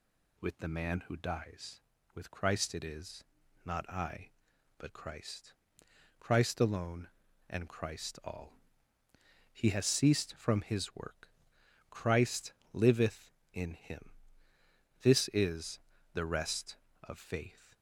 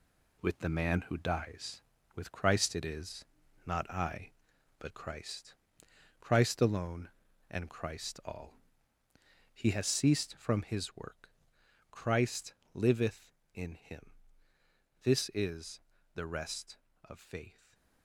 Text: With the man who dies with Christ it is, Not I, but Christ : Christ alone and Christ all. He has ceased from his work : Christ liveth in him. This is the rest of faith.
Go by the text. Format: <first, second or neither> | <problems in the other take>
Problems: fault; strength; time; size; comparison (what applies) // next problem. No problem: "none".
first | gets quieter; strong; throughout; 7.5 dB // pauses between "Christ" and "liveth"; slight; at 12.5 s; 0.18 s long; slight in the first // pauses between "is" and "the"; slight; at 15.7 s; 0.34 s long; slight in the first // stays silent after the last word; slight; from 17.5 s on; 0.5 s long